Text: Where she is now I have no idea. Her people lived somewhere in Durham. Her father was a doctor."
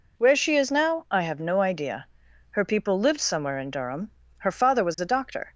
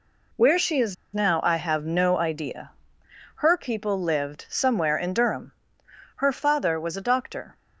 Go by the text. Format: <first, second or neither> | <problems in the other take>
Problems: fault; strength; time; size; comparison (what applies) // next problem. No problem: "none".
first | pauses between "is" and "now"; slight; at 0.9 s; 0.19 s long